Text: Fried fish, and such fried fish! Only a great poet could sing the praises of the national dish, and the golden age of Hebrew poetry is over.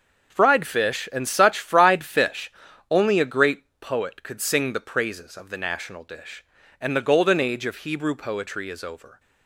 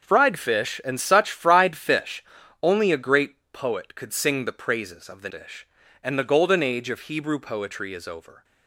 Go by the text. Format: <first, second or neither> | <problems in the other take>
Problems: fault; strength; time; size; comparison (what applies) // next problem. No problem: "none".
first | starts louder than the rest; noticeable; until 1.0 s; 6 dB; also in the first // pauses between "great" and "poet"; slight; at 3.3 s; 0.16 s long; slight in the first // skips "national"; at 5.2 s